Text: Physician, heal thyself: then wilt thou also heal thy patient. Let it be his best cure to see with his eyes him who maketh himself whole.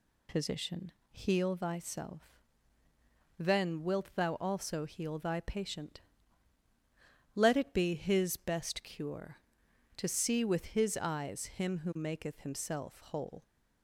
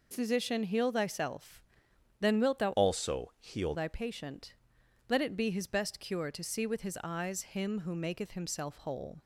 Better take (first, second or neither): first